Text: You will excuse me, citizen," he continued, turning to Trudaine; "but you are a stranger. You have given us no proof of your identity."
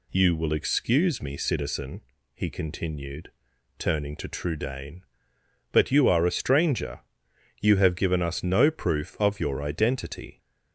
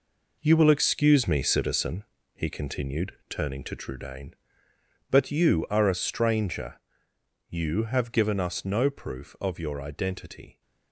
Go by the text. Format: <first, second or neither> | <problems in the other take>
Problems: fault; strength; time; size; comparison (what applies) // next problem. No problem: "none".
first | gets quieter; strong; throughout; 8.5 dB